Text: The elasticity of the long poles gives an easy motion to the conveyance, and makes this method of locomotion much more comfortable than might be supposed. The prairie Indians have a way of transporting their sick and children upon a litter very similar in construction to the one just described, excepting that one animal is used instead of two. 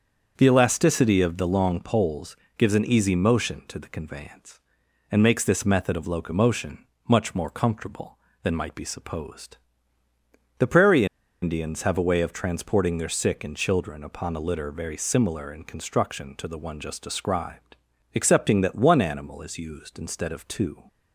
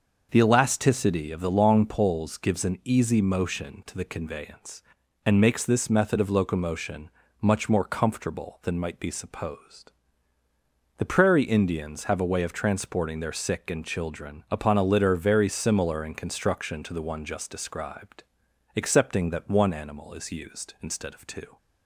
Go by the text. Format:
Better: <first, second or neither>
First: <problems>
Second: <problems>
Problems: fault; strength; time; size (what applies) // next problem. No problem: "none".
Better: second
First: starts louder than the rest; until 1.3 s; 7 dB // pauses between "poles" and "gives"; slight; at 2.3 s; 0.22 s long // pauses between "locomotion" and "much"; slight; at 6.8 s; 0.22 s long // pauses between "prairie" and "Indians"; at 11.0 s; 0.36 s long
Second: starts louder than the rest; noticeable; until 1.3 s; 6 dB // pauses between "locomotion" and "much"; slight; at 7.1 s; 0.32 s long